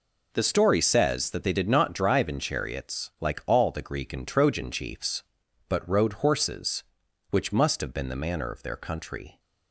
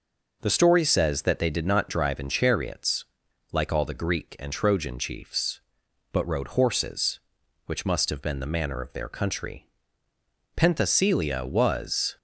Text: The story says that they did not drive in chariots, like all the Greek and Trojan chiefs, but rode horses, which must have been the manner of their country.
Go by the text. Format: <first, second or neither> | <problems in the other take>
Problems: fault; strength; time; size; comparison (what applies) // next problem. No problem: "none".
first | goes on to say "Penthesilea was"; from 10.5 s on; 1.6 s long